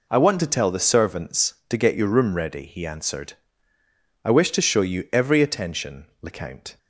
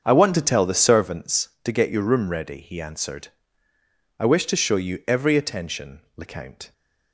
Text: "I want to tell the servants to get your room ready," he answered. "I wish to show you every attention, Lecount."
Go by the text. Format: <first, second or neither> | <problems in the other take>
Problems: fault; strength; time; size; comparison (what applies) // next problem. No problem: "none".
first | starts louder than the rest; until 1.2 s; 7 dB